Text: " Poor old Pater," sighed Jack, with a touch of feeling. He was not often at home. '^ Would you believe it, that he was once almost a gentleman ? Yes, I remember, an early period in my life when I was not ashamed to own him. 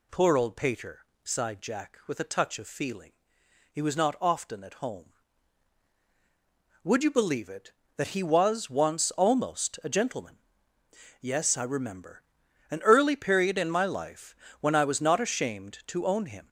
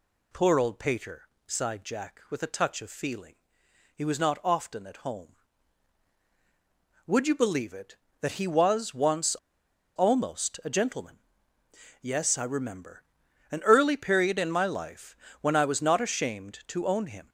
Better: first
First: pauses between "life" and "when"; slight; at 14.3 s; 0.28 s long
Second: pauses between "once" and "almost"; noticeable; at 9.3 s; 0.61 s long // pauses between "life" and "when"; slight; at 15.1 s; 0.28 s long

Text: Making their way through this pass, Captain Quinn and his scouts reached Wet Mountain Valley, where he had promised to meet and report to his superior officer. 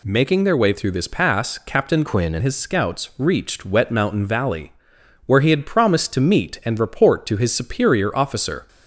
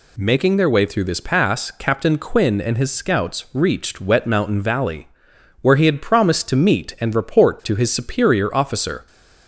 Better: second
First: changes voice from "Quinn" to "and"; from 2.0 to 2.4 s; 0.4 s long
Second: none

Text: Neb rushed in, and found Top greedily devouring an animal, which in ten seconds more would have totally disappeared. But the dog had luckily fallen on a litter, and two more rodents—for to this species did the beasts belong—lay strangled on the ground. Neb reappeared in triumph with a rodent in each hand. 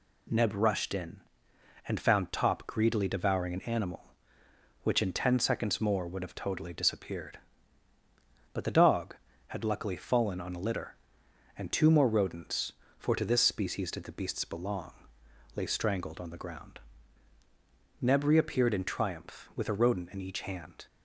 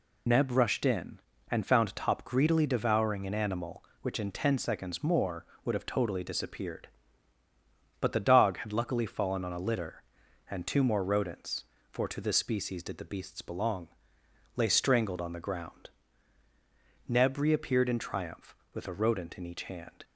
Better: first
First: none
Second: loses the start of "Neb"; at 0.2 s; 40 ms

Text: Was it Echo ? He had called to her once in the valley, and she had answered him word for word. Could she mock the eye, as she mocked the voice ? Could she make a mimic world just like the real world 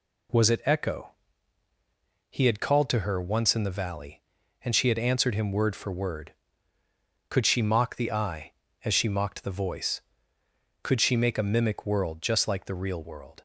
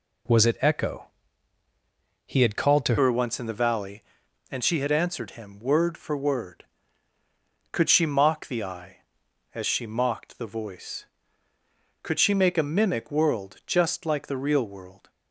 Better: first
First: none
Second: changes voice at "her"; from 2.9 s on; 12.1 s long

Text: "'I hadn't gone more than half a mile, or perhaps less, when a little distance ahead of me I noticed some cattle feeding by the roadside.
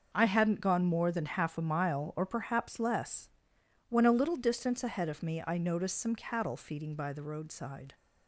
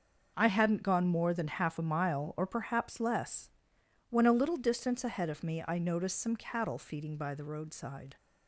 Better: neither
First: starts louder than the rest; noticeable; until 1.1 s; 6 dB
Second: starts louder than the rest; noticeable; until 1.3 s; 6 dB

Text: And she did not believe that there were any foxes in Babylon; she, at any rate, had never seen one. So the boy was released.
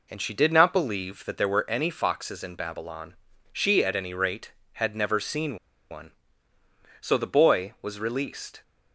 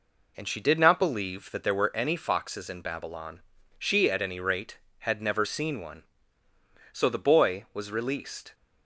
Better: second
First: pauses between "seen" and "one"; slight; at 5.5 s; 0.34 s long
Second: none

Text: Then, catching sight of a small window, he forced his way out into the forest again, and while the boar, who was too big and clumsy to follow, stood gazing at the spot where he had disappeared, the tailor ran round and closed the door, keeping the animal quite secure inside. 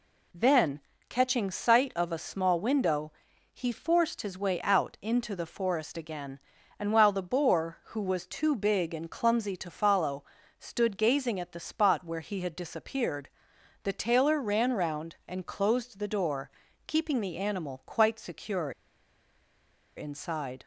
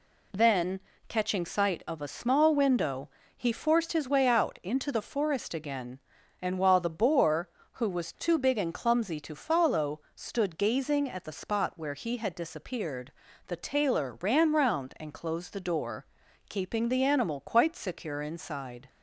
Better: second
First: pauses between "secure" and "inside"; strong; at 18.7 s; 1.2 s long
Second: none

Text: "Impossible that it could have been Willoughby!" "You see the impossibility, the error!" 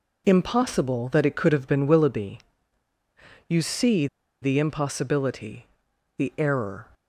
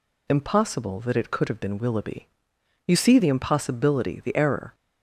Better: second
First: pauses between "see" and "the"; slight; at 4.0 s; 0.35 s long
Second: none

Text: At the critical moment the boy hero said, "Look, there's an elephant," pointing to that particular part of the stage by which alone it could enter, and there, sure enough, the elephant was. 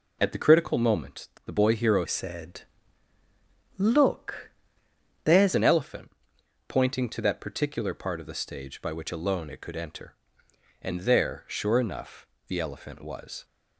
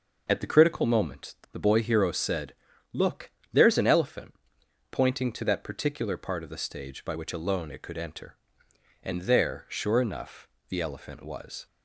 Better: second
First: pauses between "moment" and "the"; slight; at 1.2 s; 0.16 s long // changes voice from "said" to "there's"; from 2.0 to 5.5 s; 3.5 s long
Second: pauses between "moment" and "the"; slight; at 1.3 s; 0.16 s long

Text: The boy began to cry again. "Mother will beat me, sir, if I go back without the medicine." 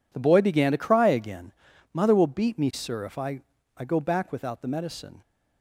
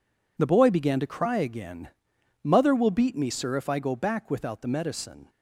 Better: second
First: says "I" twice; at 3.7 s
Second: none

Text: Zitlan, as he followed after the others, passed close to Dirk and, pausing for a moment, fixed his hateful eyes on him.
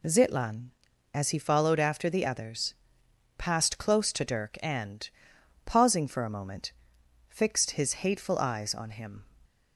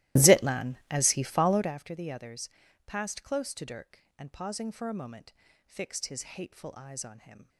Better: first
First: none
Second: starts louder than the rest; strong; until 1.7 s; 16.5 dB

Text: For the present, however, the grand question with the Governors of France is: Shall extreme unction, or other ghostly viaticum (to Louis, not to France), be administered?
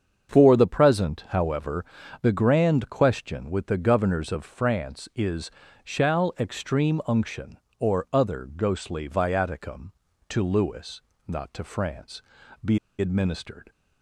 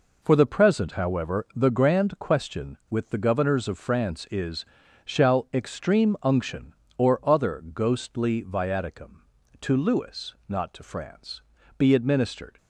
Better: second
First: starts louder than the rest; strong; until 1.3 s; 7 dB // pauses between "be" and "administered"; slight; at 12.7 s; 0.22 s long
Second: none

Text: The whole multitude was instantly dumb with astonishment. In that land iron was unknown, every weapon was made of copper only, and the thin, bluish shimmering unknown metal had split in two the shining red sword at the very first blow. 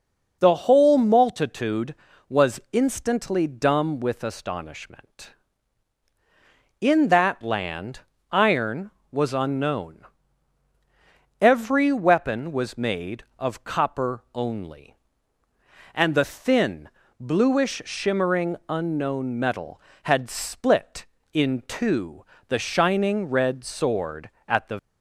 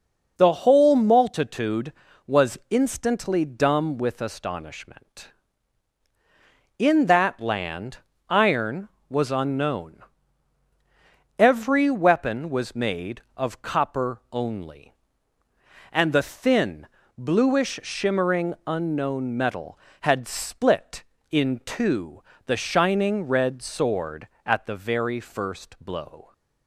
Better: second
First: pauses between "land" and "iron"; slight; at 8.0 s; 0.30 s long // pauses between "two" and "the"; slight; at 22.2 s; 0.22 s long // stops before "very first blow"; at 24.7 s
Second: pauses between "land" and "iron"; slight; at 7.9 s; 0.30 s long // pauses between "two" and "the"; slight; at 22.2 s; 0.22 s long

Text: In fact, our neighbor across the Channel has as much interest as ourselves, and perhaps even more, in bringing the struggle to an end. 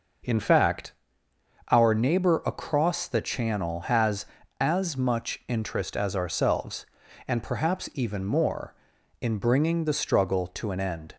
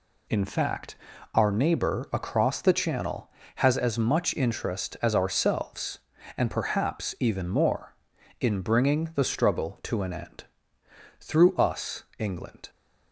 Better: first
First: none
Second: goes on to say "Through us England"; from 11.1 s on; 1.5 s long

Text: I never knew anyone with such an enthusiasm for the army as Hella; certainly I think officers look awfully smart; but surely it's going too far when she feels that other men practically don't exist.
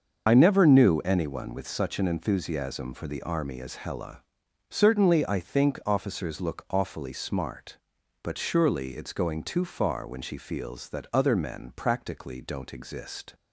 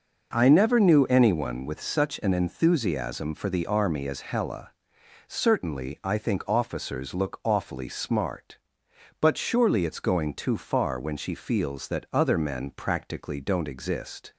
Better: second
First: loses the start of "I"; at 0.2 s; 40 ms // starts louder than the rest; until 1.2 s; 6.5 dB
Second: none

